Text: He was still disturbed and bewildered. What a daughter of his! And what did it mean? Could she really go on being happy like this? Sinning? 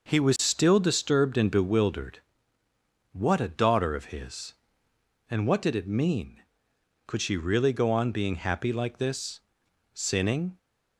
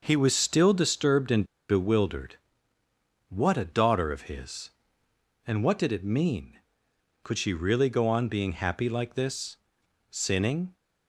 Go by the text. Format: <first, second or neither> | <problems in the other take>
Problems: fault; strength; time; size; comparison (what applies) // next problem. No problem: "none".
first | pauses between "and" and "bewildered"; slight; at 1.4 s; 0.23 s long